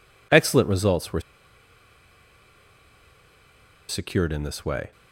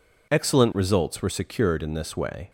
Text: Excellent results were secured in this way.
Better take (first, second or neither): second